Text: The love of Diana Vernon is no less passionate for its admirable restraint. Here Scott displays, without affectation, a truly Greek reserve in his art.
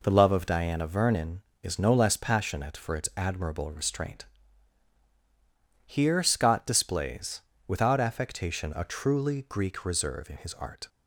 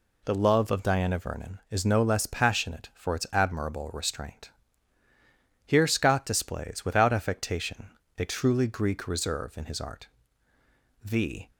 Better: first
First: none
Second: goes on to say "The"; slight; from 11.0 s on; 0.48 s long

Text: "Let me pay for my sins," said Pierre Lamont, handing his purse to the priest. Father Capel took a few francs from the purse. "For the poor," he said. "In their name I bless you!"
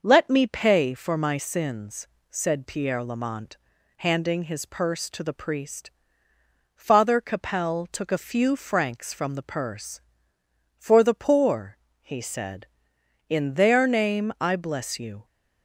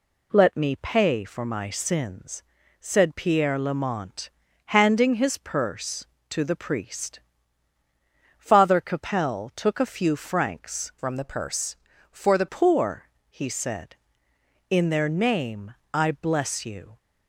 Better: first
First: none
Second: changes voice from "from" to "the"; from 10.9 to 12.4 s; 1.5 s long // pauses between "name" and "I"; slight; at 15.7 s; 0.18 s long

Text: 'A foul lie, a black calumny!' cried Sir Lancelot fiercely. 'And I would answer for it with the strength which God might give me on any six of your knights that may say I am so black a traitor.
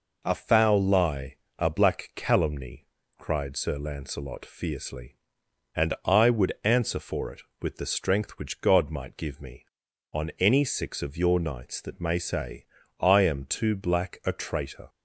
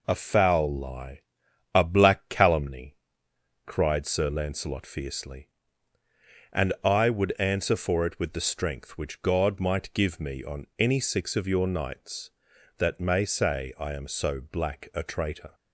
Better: second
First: pauses between "say" and "I"; slight; at 12.6 s; 0.34 s long // says "too" for "so"; at 13.4 s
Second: none

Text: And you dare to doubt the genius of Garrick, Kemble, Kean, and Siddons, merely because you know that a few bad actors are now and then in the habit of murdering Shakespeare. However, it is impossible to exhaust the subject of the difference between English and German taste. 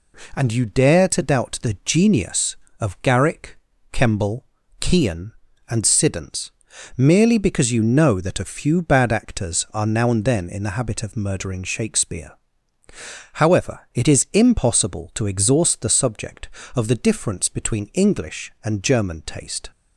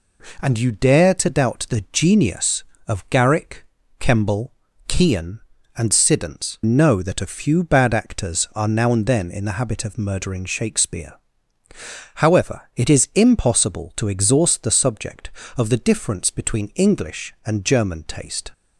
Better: first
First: none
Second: skips "merely because you"; at 6.6 s

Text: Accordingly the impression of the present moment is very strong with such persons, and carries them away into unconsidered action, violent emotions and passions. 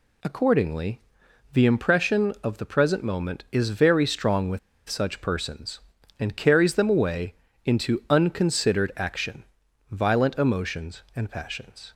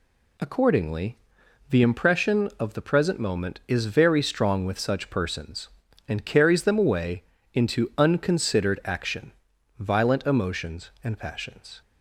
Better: second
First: pauses between "Accordingly" and "the"; noticeable; at 0.9 s; 0.54 s long // pauses between "with" and "such"; slight; at 4.5 s; 0.29 s long // pauses between "away" and "into"; slight; at 7.3 s; 0.30 s long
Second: pauses between "Accordingly" and "the"; noticeable; at 1.1 s; 0.54 s long // pauses between "away" and "into"; slight; at 7.2 s; 0.30 s long

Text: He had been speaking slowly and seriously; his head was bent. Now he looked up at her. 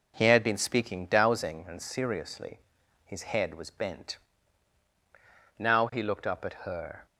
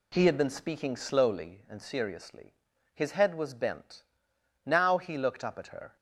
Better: second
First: says "dowsing" for "slowly"; at 1.0 s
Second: none

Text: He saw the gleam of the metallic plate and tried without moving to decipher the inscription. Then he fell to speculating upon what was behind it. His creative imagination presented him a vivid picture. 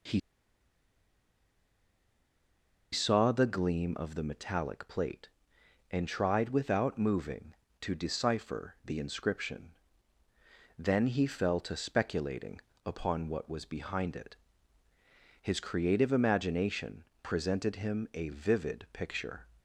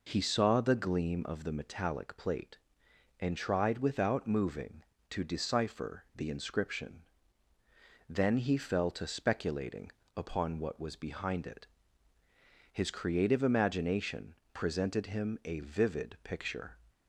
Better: second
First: pauses between "He" and "saw"; strong; at 0.1 s; 2.7 s long // pauses between "speculating" and "upon"; slight; at 12.6 s; 0.26 s long // pauses between "imagination" and "presented"; slight; at 17.0 s; 0.18 s long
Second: pauses between "speculating" and "upon"; slight; at 9.9 s; 0.26 s long // pauses between "imagination" and "presented"; slight; at 14.3 s; 0.18 s long

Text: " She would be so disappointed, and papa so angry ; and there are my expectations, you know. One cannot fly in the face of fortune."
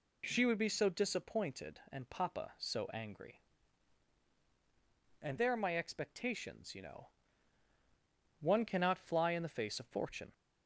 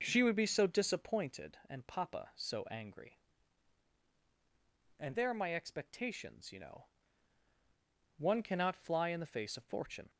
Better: first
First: none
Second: starts louder than the rest; noticeable; until 1.4 s; 5.5 dB

